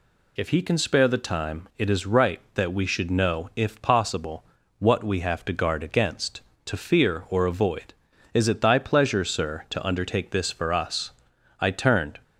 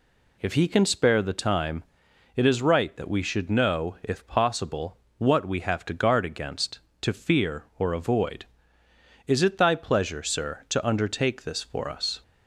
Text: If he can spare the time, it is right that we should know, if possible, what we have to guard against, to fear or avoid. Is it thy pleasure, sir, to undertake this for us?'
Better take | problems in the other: second | goes on to say "I turned"; from 11.5 s on; 0.60 s long

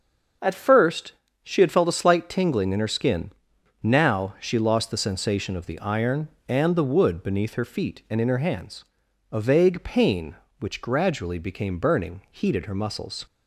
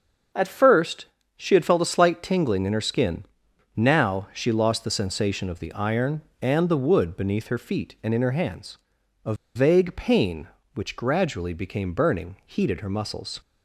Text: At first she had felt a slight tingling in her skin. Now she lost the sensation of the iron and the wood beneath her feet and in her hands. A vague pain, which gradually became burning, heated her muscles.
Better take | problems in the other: first | starts louder than the rest; until 1.6 s; 6.5 dB; also in the first // pauses between "first" and "she"; slight; at 1.0 s; 0.32 s long; slight in the first // pauses between "A" and "vague"; slight; at 9.3 s; 0.20 s long

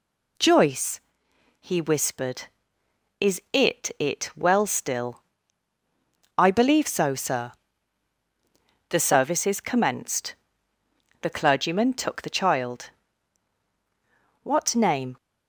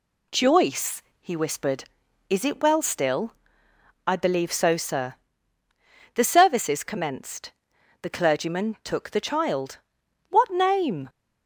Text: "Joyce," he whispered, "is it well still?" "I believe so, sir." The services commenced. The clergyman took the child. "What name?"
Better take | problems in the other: second | says "it" twice; at 3.9 s

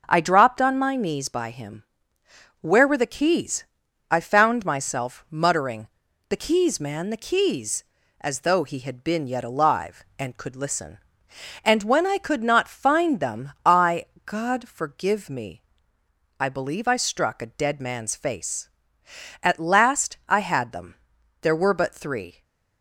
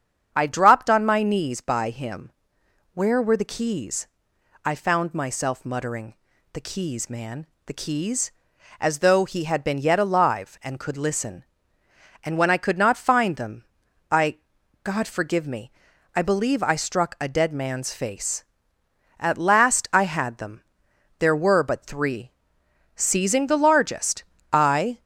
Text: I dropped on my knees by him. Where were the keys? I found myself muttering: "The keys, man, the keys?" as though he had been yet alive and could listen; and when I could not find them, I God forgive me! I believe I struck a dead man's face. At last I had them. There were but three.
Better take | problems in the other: first | starts louder than the rest; strong; until 1.3 s; 7.5 dB // pauses between "I" and "God"; noticeable; at 14.3 s; 0.46 s long; slight in the first // goes on to say "Seizing the largest I"; strong; from 22.9 s on; 2.0 s long

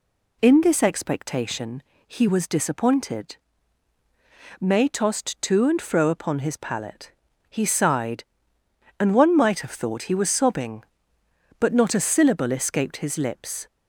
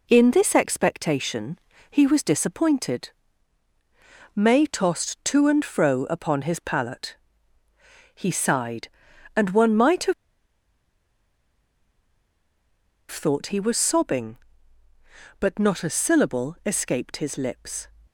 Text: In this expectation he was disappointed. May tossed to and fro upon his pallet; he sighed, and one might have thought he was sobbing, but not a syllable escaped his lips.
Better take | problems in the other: first | pauses between "expectation" and "he"; slight; at 1.5 s; 0.32 s long; slight in the first // pauses between "have" and "thought"; strong; at 10.1 s; 2.9 s long

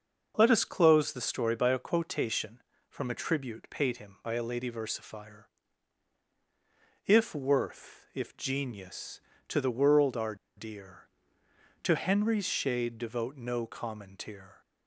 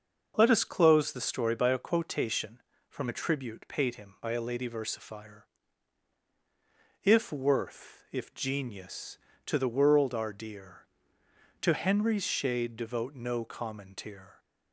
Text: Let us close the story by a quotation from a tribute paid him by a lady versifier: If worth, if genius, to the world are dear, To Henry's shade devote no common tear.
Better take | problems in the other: second | starts louder than the rest; until 1.3 s; 6.5 dB; also in the second // pauses between "are" and "dear"; slight; at 10.3 s; 0.21 s long

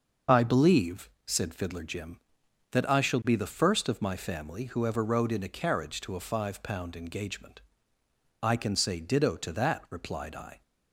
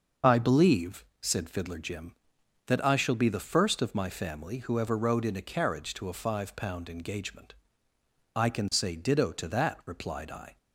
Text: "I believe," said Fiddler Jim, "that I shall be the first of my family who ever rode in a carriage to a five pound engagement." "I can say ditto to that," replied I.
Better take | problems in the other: neither | starts louder than the rest; the same in both

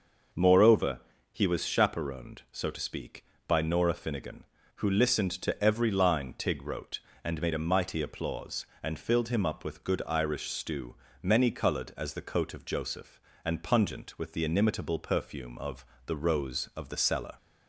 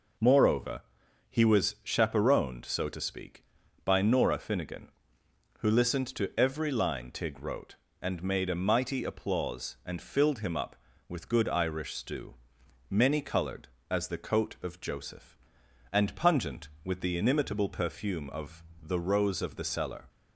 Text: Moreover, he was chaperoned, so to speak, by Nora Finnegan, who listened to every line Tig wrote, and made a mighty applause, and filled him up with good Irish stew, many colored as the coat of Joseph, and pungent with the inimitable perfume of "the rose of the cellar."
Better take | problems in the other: neither | pauses between "of" and "the"; slight; the same in both

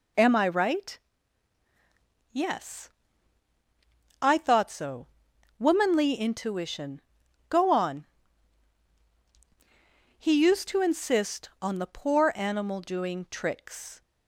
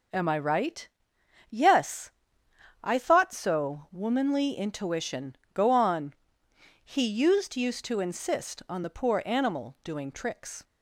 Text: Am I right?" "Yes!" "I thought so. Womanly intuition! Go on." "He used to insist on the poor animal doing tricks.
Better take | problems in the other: first | says "used" twice; at 7.5 s

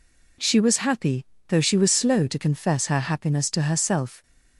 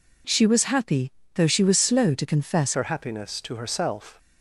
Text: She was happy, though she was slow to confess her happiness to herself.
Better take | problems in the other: first | changes voice at "her"; from 2.7 s on; 1.4 s long

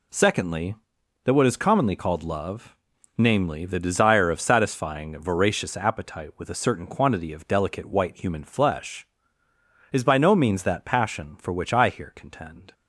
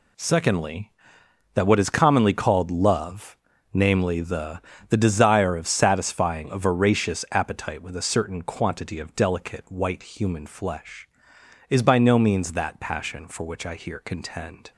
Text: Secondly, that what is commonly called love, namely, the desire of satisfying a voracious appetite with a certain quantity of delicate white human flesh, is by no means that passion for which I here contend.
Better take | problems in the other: first | says "the" twice; at 4.8 s

